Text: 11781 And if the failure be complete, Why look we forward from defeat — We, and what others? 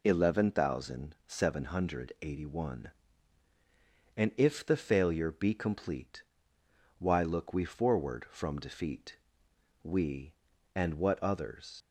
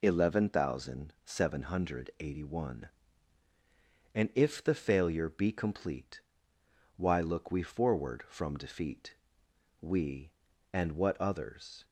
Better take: second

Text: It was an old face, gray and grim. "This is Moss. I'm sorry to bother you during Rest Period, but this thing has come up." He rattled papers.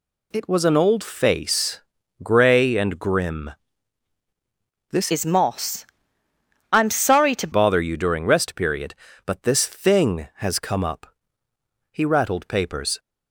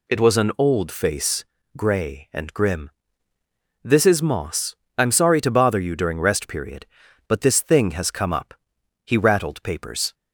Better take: second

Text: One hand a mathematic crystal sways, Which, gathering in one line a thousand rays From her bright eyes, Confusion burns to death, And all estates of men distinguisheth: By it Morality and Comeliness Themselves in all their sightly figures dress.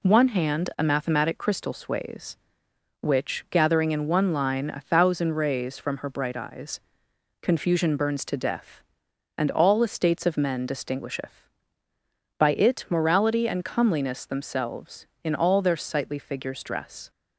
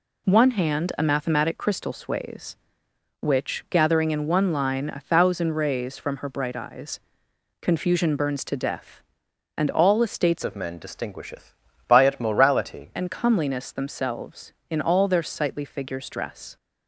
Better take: first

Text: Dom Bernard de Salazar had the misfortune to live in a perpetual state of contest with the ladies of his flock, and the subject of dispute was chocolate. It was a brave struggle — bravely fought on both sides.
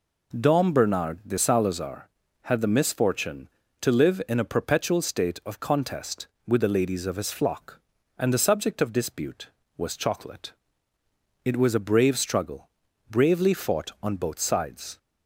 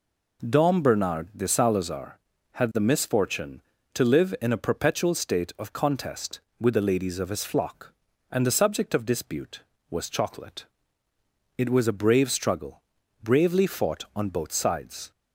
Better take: neither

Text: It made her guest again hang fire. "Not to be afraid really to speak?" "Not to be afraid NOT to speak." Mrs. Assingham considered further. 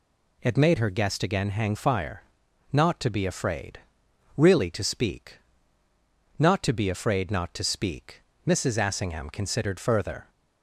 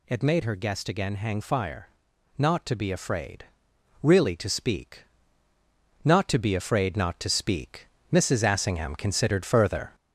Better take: first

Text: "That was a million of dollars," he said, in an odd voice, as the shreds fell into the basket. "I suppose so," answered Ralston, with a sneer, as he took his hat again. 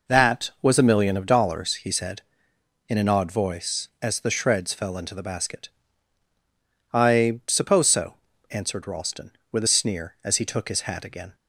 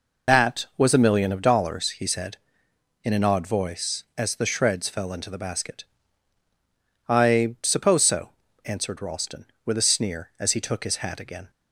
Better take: first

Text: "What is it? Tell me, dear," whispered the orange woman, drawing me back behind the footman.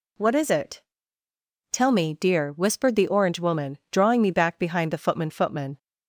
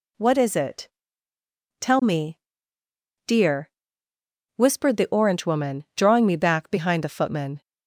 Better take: second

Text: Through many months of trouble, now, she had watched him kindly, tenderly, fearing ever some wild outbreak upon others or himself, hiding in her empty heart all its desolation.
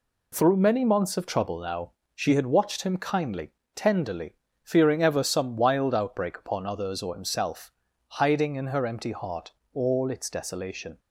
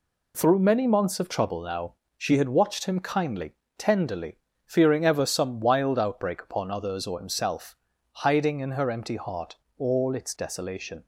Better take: neither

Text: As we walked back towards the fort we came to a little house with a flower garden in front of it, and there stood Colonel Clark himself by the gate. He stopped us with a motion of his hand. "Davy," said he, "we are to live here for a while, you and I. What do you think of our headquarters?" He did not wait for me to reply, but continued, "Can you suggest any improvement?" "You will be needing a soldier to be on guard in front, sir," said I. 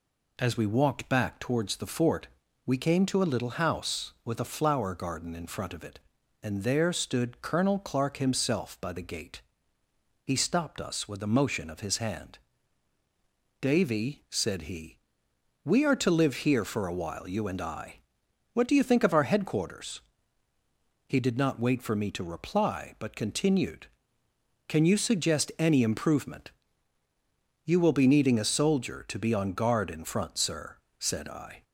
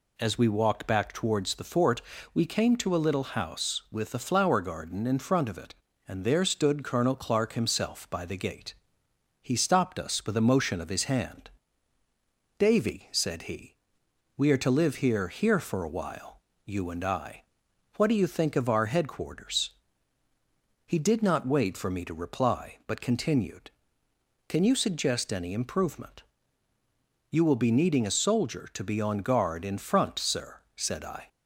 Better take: first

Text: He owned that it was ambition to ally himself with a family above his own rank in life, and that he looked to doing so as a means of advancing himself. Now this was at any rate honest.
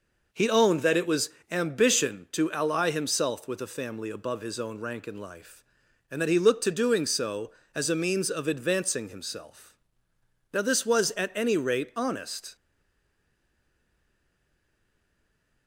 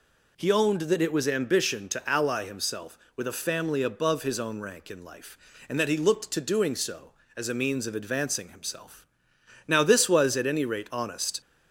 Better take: second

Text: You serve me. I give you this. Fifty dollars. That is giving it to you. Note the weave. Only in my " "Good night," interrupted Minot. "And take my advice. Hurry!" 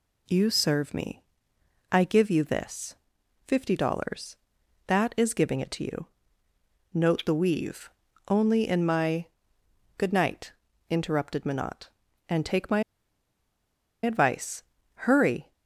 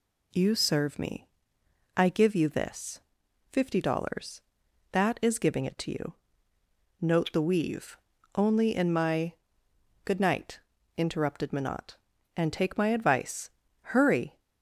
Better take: second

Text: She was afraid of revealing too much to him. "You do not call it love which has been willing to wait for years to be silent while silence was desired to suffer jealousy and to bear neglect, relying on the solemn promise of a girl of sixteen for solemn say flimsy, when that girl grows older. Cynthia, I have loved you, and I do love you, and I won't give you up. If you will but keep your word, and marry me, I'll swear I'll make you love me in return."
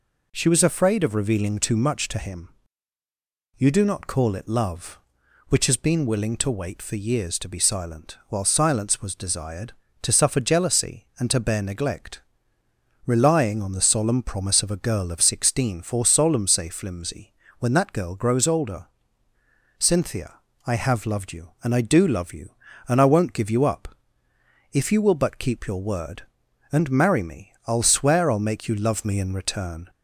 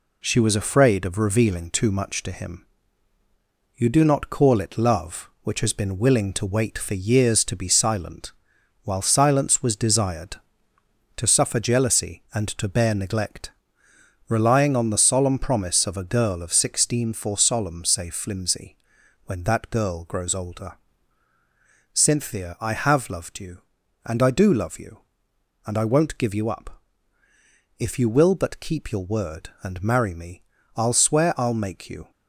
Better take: first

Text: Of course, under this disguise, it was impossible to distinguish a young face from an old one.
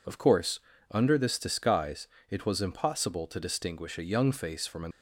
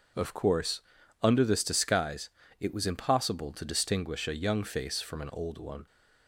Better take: second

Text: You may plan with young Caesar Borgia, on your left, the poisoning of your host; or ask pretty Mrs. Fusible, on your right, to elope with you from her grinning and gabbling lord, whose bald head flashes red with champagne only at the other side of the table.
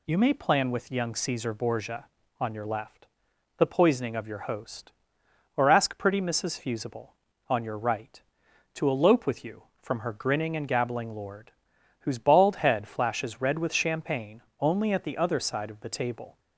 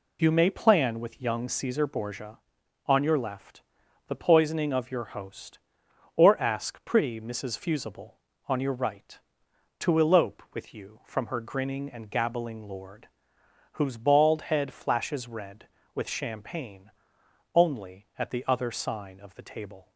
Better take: first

